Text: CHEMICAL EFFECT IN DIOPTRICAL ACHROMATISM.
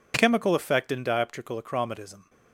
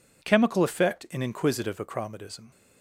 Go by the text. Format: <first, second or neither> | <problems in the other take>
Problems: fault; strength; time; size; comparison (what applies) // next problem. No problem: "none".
first | says "Inquisitive" for "DIOPTRICAL"; at 1.1 s